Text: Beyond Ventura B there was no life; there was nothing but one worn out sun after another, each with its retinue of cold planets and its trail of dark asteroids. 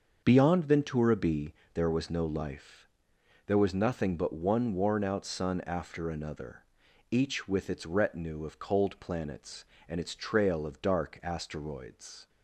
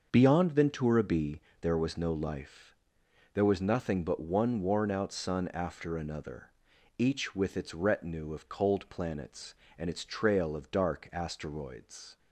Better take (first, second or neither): neither